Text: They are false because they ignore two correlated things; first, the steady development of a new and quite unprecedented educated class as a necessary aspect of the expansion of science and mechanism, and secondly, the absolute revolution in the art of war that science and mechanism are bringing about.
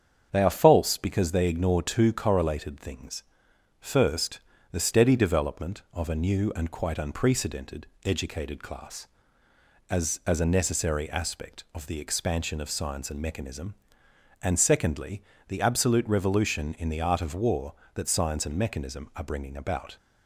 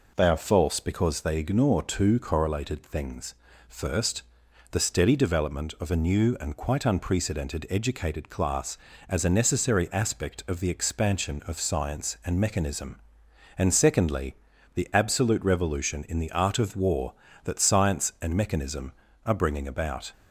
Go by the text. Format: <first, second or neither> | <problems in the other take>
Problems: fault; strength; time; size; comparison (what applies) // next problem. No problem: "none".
second | starts louder than the rest; strong; until 1.3 s; 7.5 dB // pauses between "unprecedented" and "educated"; slight; at 7.8 s; 0.18 s long // says "as" twice; at 10.2 s